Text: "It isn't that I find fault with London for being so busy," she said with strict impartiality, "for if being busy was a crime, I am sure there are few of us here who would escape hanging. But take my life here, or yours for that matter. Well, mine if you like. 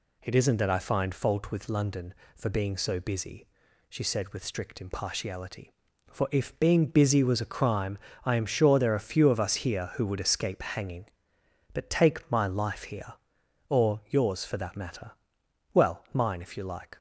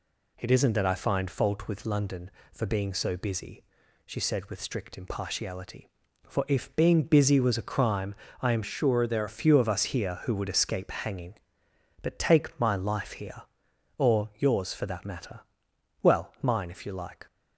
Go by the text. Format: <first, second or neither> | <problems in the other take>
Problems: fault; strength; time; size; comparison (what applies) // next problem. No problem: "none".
first | changes voice from "sure" to "there"; from 8.6 to 9.2 s; 0.6 s long